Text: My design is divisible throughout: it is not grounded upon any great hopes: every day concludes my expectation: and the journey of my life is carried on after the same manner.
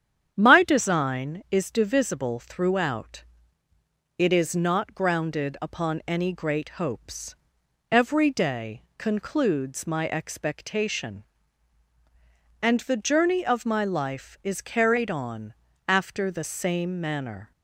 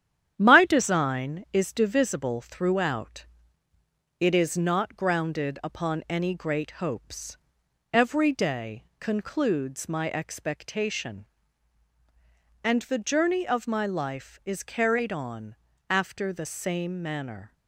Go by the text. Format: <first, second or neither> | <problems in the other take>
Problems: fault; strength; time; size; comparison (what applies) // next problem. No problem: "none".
first | gets quieter; noticeable; throughout; 4.5 dB // starts louder than the rest; strong; until 1.3 s; 10 dB; strong in the first // pauses between "day" and "concludes"; slight; at 8.8 s; 0.16 s long; slight in the first // pauses between "on" and "after"; slight; at 15.5 s; 0.34 s long; slight in the first